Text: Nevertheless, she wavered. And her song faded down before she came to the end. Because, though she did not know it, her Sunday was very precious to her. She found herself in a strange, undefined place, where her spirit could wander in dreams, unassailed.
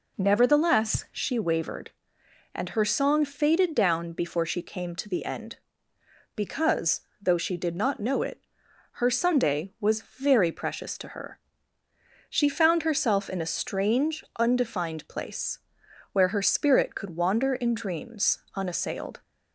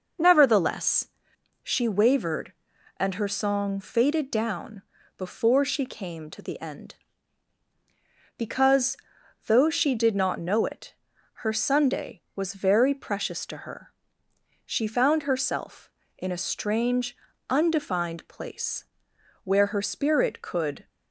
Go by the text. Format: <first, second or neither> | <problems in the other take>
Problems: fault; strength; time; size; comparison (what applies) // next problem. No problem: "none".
first | pauses between "down" and "before"; slight; at 4.8 s; 0.34 s long // stops before "wander in dreams unassailed"; at 20.8 s